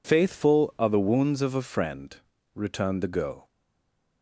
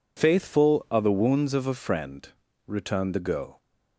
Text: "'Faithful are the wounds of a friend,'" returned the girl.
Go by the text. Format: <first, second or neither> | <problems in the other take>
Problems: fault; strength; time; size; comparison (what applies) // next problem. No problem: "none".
second | stays silent after the last word; slight; from 3.4 s on; 0.8 s long